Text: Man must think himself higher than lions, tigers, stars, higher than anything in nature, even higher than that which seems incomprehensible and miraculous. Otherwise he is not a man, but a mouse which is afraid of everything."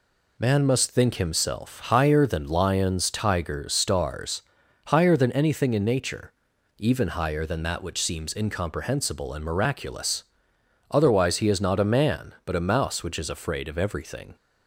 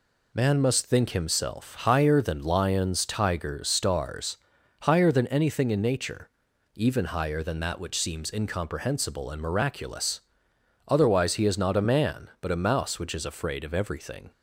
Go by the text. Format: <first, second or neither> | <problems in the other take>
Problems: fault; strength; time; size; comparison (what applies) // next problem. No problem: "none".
neither | none